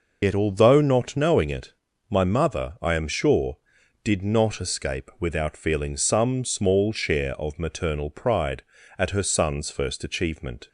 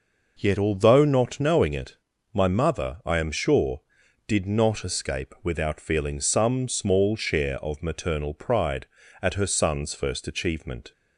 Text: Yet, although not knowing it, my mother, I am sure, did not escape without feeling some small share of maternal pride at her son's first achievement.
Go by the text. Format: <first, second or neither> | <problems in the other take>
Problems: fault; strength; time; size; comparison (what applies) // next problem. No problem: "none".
second | loses the start of "Yet"; at 0.2 s; 85 ms